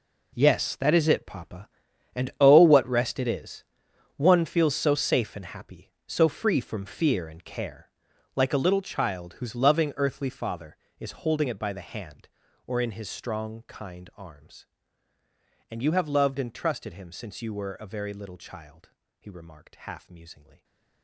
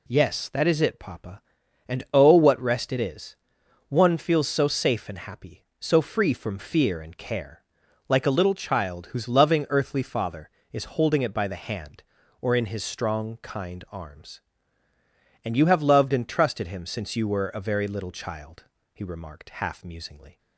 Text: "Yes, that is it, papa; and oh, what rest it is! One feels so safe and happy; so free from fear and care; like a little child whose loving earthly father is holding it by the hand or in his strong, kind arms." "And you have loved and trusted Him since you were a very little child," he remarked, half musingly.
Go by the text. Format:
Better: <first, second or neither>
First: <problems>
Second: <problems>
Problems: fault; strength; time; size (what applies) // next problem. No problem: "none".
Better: second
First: gets quieter; strong; throughout; 14.5 dB // stays silent after the last word; slight; from 20.4 s on; 0.6 s long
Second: none